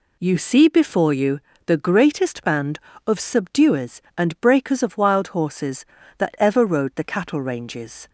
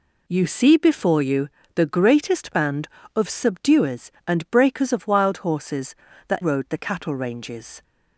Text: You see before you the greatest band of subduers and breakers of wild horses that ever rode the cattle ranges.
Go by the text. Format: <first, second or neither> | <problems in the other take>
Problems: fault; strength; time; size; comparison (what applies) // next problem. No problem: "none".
first | pauses between "you" and "the"; slight; at 1.4 s; 0.26 s long; slight in the first // skips "ever"; at 6.4 s